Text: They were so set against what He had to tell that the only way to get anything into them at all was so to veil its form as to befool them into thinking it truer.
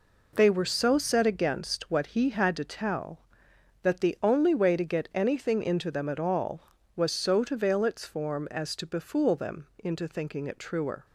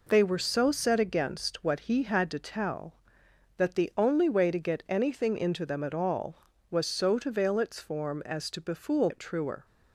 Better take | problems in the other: first | skips "them into thinking"; at 9.0 s

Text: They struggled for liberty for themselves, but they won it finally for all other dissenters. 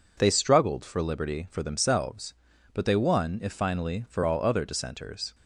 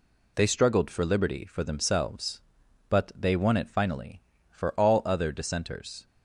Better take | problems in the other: second | says "if" for "it"; at 3.4 s

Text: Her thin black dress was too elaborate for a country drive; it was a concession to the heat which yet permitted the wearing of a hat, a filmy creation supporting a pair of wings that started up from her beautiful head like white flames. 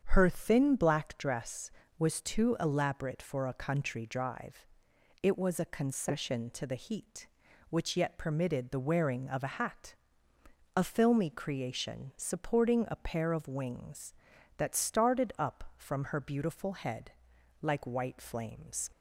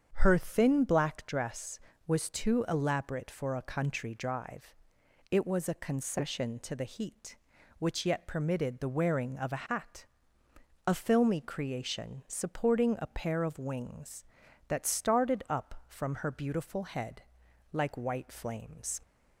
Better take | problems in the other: neither | starts louder than the rest; strong; the same in both // pauses between "head" and "like"; noticeable; the same in both

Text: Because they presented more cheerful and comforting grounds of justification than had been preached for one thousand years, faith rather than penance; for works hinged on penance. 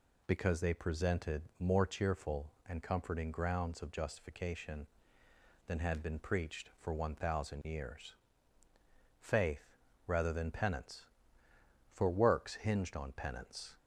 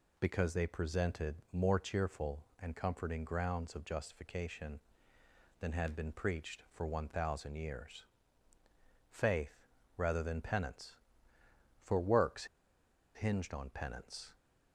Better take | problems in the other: first | pauses between "presented" and "more"; slight; at 1.3 s; 0.18 s long; slight in the first // pauses between "faith" and "rather"; slight; at 9.6 s; 0.28 s long; slight in the first // pauses between "works" and "hinged"; noticeable; at 12.4 s; 0.70 s long

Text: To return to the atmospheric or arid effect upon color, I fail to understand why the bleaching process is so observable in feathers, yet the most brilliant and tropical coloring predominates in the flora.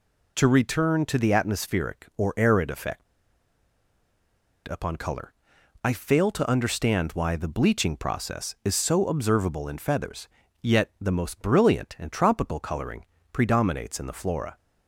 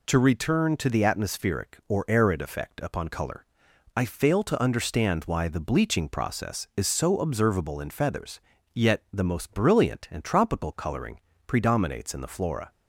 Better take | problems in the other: second | pauses between "effect" and "upon"; strong; at 3.0 s; 1.6 s long // pauses between "coloring" and "predominates"; slight; at 13.0 s; 0.26 s long; slight in the second

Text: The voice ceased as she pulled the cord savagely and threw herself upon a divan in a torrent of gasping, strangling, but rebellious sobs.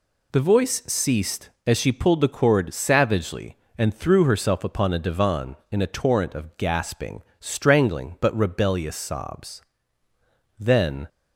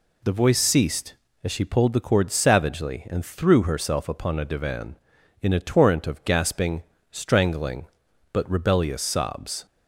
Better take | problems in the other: second | goes on to say "Then"; from 10.5 s on; 0.50 s long

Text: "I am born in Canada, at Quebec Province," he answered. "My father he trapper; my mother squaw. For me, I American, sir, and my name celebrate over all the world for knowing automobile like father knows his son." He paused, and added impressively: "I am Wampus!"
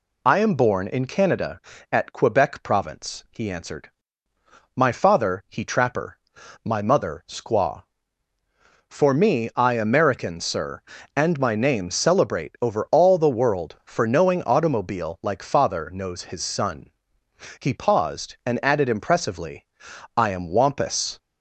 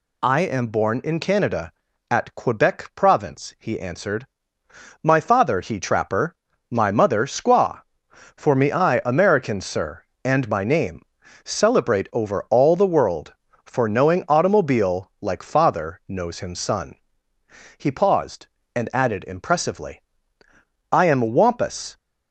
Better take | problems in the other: first | pauses between "name" and "celebrate"; at 11.0 s; 0.42 s long // says "him" for "his"; at 16.4 s

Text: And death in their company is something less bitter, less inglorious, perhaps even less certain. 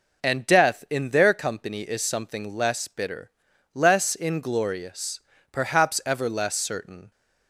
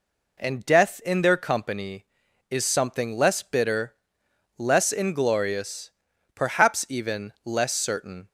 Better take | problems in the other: second | says "ever" for "even"; at 6.0 s

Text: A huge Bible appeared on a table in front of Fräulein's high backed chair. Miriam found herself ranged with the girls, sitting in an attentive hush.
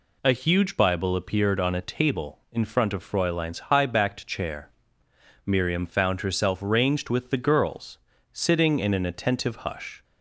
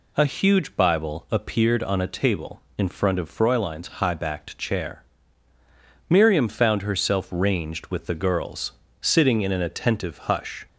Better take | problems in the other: neither | none

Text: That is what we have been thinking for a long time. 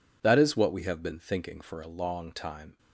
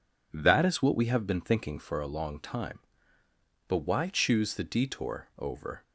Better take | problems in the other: first | goes on to say "But why choose the detour over"; strong; from 3.6 s on; 2.1 s long

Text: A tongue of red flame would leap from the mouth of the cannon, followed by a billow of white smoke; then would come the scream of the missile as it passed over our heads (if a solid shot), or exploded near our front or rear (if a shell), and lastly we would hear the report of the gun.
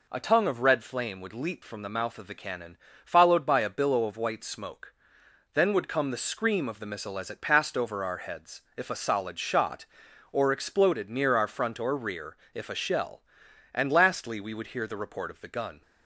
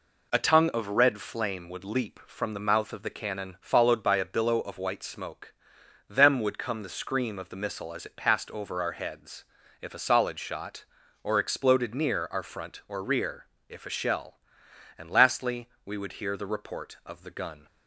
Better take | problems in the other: first | says "them" for "then"; at 6.0 s // pauses between "lastly" and "we"; slight; at 15.6 s; 0.16 s long

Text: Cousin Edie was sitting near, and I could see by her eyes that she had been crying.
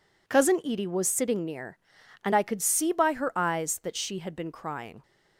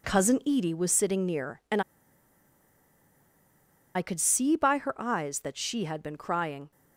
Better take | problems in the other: first | pauses between "and" and "I"; strong; at 1.8 s; 2.1 s long

